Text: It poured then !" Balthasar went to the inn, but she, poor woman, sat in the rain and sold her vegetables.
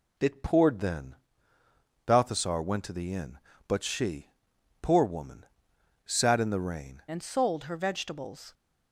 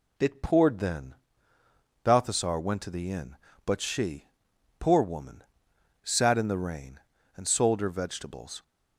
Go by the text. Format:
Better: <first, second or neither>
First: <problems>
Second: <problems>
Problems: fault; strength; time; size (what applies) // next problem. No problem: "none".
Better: second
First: changes voice at "and"; from 7.0 s on; 1.5 s long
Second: none